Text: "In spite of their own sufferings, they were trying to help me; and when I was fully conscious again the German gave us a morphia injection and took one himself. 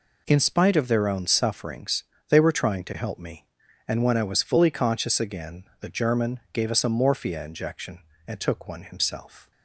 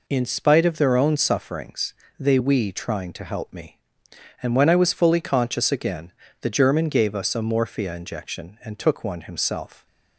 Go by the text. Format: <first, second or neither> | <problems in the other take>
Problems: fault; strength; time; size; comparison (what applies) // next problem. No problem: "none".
first | says "we" for "were"; at 2.3 s // pauses between "again" and "the"; slight; at 6.1 s; 0.30 s long; slight in the first